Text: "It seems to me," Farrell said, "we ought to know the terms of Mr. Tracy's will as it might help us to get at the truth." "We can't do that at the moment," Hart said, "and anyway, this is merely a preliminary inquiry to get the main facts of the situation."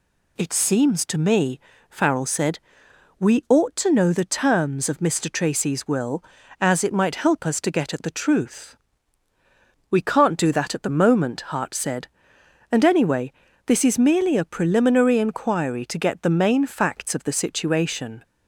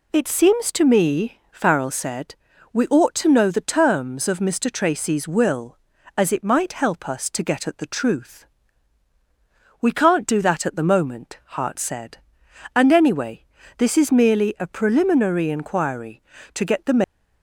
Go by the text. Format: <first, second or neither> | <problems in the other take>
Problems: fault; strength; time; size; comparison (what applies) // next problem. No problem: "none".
first | stops before "main facts of the situation"; at 17.0 s